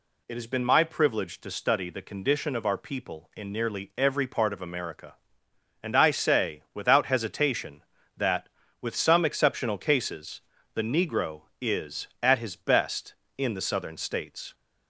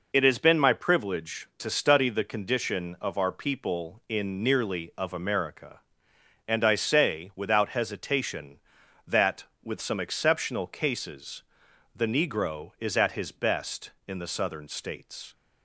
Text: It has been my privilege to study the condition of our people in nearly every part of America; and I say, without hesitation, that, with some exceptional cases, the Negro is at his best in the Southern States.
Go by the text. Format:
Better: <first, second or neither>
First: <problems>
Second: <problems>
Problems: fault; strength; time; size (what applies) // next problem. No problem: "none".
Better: first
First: none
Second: skips "every part"; at 4.9 s